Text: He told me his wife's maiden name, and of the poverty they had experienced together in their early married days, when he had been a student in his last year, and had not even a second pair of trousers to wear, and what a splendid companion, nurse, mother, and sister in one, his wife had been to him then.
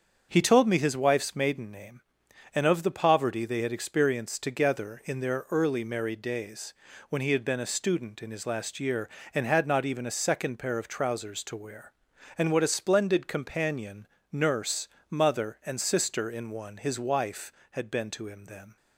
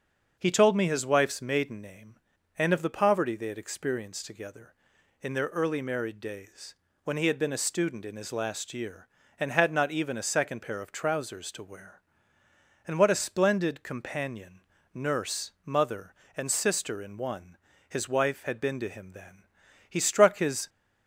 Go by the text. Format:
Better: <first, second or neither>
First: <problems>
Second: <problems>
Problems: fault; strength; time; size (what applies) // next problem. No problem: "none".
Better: first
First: starts louder than the rest; until 1.3 s; 7 dB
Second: starts louder than the rest; until 1.3 s; 6.5 dB // goes on to say "He struck his"; noticeable; from 19.8 s on; 0.80 s long